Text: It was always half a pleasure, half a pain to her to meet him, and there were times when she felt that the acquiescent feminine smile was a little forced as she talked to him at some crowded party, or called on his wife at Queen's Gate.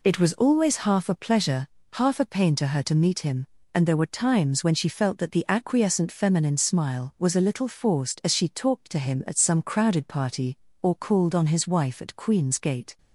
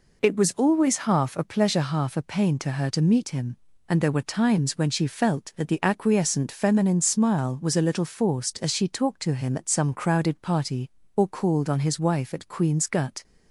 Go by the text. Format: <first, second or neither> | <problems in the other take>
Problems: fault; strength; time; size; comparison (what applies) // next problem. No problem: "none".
first | says "Gut" for "Gate"; at 12.8 s